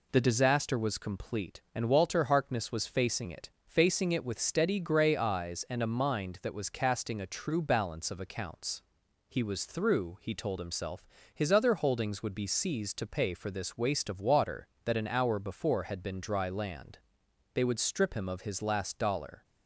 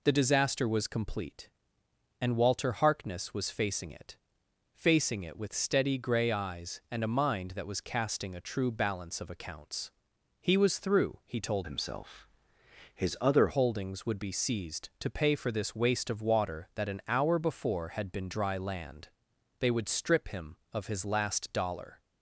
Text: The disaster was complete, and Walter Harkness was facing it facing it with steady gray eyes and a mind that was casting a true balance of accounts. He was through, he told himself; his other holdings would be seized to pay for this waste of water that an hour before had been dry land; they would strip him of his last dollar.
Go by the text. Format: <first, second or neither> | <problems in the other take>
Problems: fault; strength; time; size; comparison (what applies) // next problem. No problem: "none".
first | pauses between "it" and "facing"; noticeable; at 4.1 s; 0.56 s long; slight in the first // changes voice from "himself" to "other"; from 11.6 to 13.4 s; 1.8 s long